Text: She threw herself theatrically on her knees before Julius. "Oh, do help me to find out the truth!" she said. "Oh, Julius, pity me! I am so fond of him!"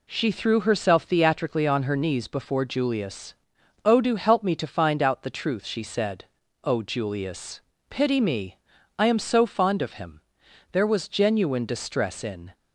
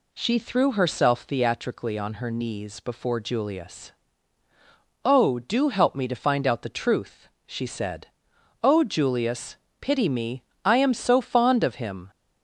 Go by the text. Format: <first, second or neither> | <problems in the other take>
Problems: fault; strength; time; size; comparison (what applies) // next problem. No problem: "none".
second | goes on to say "There was genuine distress in"; strong; from 10.7 s on; 1.8 s long